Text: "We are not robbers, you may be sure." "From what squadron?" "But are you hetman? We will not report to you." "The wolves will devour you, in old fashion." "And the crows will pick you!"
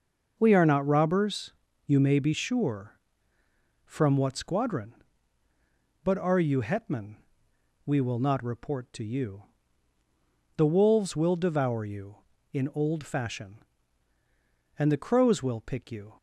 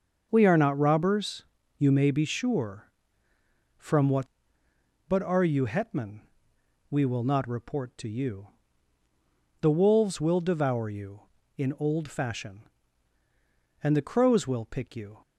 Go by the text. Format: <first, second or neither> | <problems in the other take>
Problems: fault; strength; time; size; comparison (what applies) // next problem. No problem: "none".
first | starts louder than the rest; until 1.3 s; 6.5 dB // skips "squadron"; at 4.6 s